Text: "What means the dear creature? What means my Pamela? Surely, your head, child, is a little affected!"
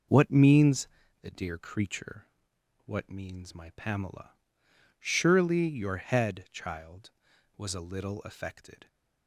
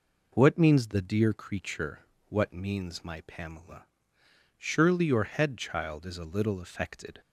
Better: second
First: pauses between "means" and "the"; slight; at 0.8 s; 0.34 s long // says "was" for "is"; at 7.5 s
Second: none

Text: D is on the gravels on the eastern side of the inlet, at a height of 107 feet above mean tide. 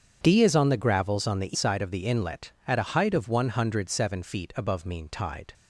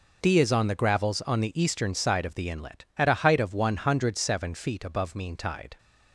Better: second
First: starts louder than the rest; strong; until 1.2 s; 8 dB // skips "eastern"; at 1.5 s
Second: none

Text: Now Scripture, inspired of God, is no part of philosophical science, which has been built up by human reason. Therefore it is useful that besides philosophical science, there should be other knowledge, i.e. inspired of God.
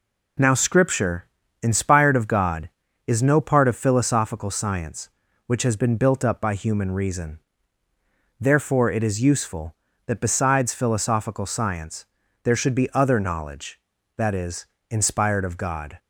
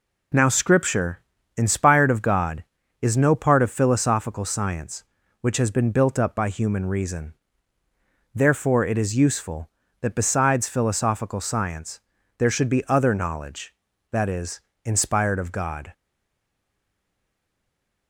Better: first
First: none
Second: stays silent after the last word; from 15.9 s on; 2.1 s long

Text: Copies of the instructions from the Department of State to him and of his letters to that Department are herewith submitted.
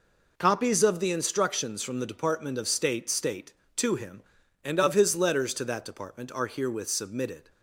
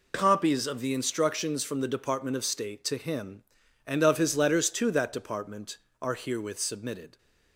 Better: second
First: says "State" twice; at 3.0 s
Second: none

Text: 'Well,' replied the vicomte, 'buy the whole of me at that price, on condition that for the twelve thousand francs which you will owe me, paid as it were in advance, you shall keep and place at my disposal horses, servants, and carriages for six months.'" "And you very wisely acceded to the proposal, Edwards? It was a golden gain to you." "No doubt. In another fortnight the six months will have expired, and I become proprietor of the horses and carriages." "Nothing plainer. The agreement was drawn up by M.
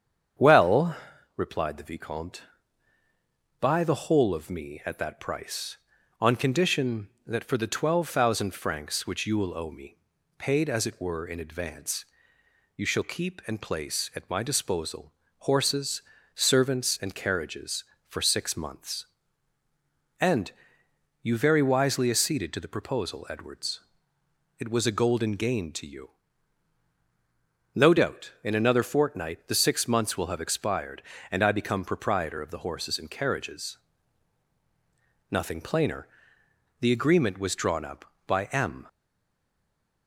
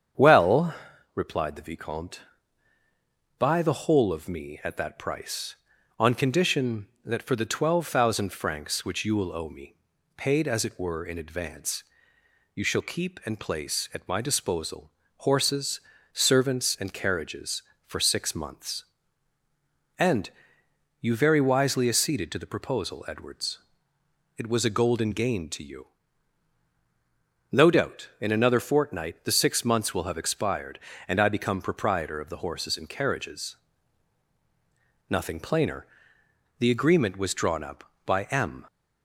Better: second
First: starts louder than the rest; strong; until 1.7 s; 8 dB // pauses between "disposal" and "horses"; slight; at 15.1 s; 0.30 s long // pauses between "And" and "you"; noticeable; at 20.5 s; 0.72 s long // stays silent after the last word; noticeable; from 38.8 s on; 1.2 s long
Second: starts louder than the rest; strong; until 1.5 s; 8 dB // pauses between "disposal" and "horses"; slight; at 14.8 s; 0.30 s long // pauses between "And" and "you"; noticeable; at 20.2 s; 0.72 s long

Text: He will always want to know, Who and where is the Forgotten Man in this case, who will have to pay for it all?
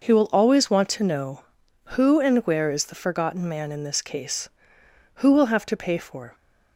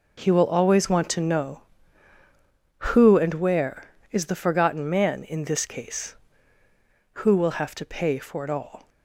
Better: second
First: stops before "it all"; at 6.3 s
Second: none

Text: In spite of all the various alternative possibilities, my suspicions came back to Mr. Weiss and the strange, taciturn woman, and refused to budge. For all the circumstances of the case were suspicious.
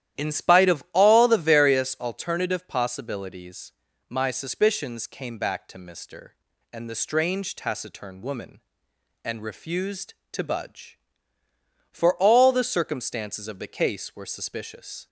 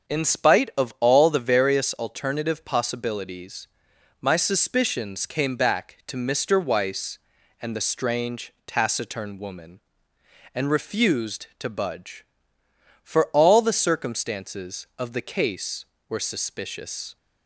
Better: second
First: starts louder than the rest; strong; until 1.3 s; 12 dB // skips "Weiss"; at 6.5 s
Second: starts louder than the rest; strong; until 1.2 s; 7 dB

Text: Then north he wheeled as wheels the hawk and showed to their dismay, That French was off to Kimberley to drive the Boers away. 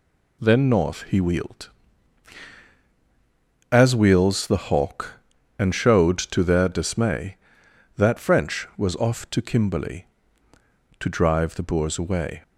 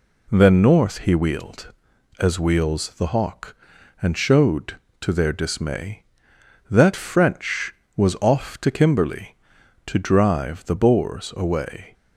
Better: neither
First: none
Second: none

